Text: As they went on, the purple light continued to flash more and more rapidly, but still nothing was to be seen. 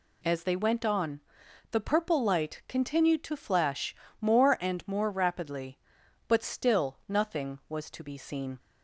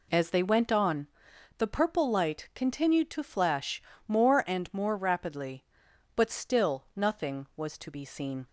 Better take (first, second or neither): first